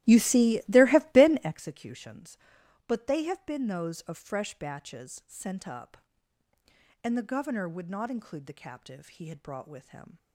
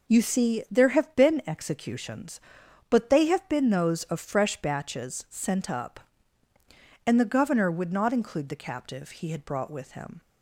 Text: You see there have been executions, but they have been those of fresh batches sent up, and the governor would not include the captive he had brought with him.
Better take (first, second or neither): second